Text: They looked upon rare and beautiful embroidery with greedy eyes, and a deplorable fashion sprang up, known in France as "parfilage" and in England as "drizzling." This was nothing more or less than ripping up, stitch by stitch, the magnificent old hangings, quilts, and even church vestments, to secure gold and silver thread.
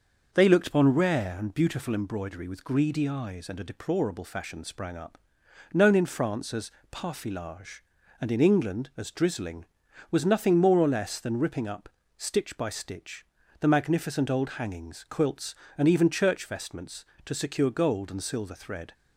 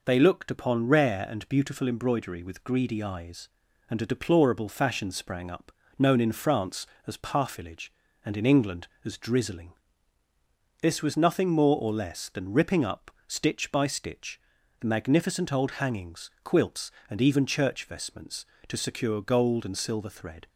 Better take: second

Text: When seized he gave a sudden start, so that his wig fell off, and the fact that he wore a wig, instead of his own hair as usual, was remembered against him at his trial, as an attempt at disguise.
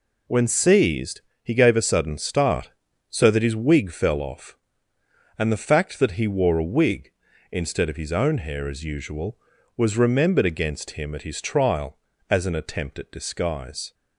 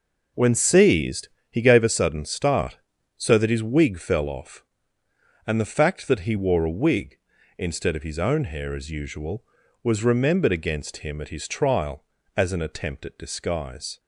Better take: first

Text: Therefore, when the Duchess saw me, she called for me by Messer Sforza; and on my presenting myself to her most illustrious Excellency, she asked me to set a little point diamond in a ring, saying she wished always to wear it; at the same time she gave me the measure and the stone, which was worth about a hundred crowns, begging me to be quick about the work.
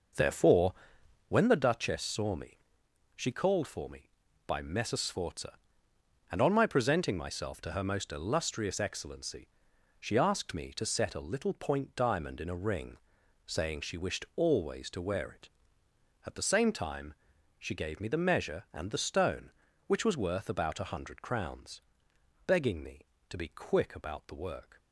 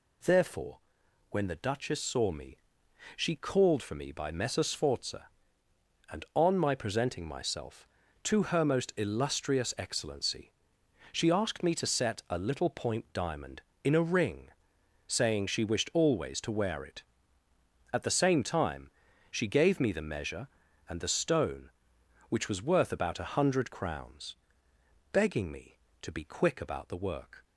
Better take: second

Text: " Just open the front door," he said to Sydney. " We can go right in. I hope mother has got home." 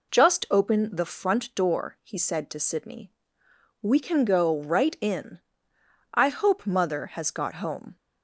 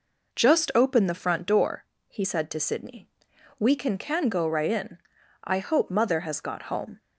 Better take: first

